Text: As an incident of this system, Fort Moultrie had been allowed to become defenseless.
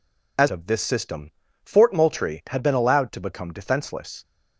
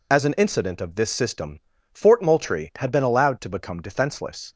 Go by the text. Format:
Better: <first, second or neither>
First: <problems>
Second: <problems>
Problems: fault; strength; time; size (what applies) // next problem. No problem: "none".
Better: second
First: skips "an incident"; at 0.4 s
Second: none